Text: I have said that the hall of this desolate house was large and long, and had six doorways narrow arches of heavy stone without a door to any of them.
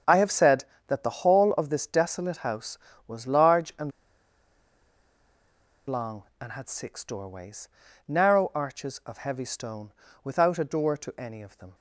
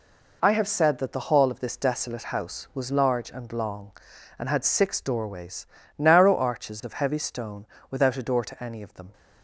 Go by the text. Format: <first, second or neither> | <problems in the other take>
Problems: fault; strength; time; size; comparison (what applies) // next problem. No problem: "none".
second | starts louder than the rest; strong; until 1.3 s; 7.5 dB // pauses between "and" and "long"; strong; at 3.9 s; 1.9 s long // pauses between "doorways" and "narrow"; at 7.6 s; 0.40 s long; slight in the second // pauses between "stone" and "without"; slight; at 9.9 s; 0.32 s long; slight in the second